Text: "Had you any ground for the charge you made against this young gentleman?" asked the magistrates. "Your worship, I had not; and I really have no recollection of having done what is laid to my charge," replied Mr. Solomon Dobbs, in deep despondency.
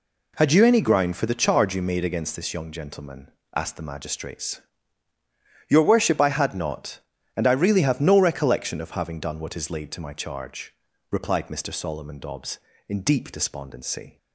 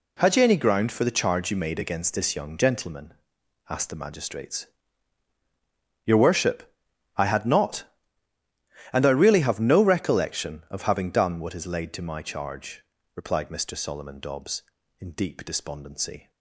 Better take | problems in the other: neither | none

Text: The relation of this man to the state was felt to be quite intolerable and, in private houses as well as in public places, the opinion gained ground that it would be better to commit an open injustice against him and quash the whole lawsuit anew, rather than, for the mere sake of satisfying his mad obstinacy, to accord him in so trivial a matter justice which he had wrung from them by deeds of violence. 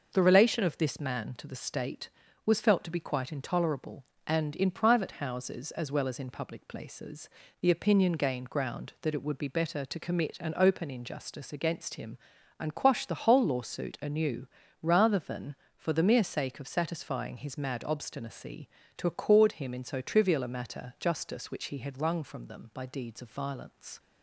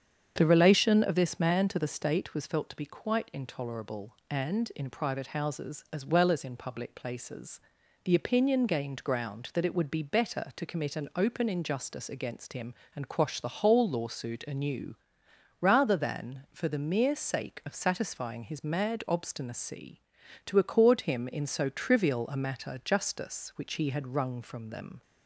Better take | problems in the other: first | starts louder than the rest; strong; until 1.3 s; 7.5 dB // stops before "by deeds of violence"; at 25.0 s

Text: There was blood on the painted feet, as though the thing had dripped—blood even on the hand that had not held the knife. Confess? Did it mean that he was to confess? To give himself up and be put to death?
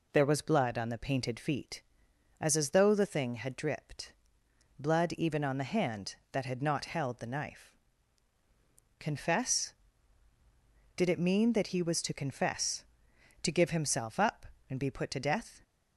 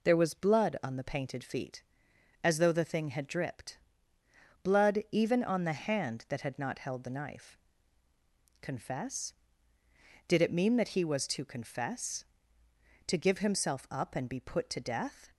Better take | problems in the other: second | says "as" twice; at 2.5 s

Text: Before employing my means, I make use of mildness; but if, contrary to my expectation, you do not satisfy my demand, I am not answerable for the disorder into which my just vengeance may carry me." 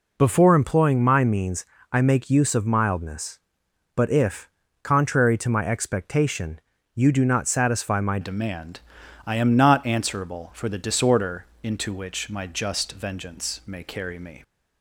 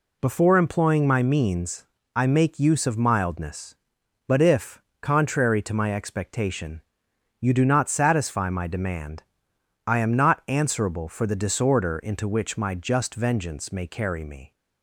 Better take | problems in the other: second | changes voice at "demand"; from 8.2 s on; 6.2 s long // pauses between "disorder" and "into"; slight; at 11.4 s; 0.18 s long

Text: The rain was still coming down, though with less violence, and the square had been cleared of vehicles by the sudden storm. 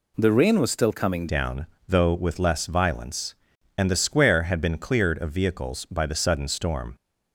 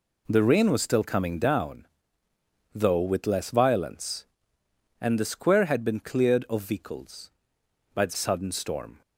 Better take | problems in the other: second | changes voice at "down"; from 1.2 s on; 5.7 s long

